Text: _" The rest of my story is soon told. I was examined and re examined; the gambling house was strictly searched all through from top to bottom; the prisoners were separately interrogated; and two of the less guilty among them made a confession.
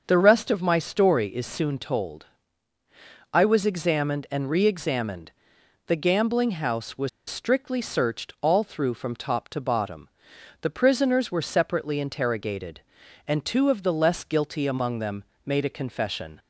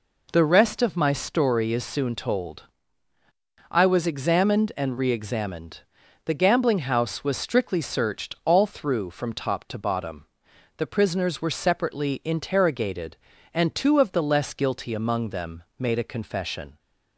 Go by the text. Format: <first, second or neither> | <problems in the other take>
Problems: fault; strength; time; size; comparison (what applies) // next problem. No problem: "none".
second | starts louder than the rest; until 1.0 s; 6.5 dB // pauses between "was" and "strictly"; slight; at 7.0 s; 0.18 s long // pauses between "them" and "made"; slight; at 15.2 s; 0.20 s long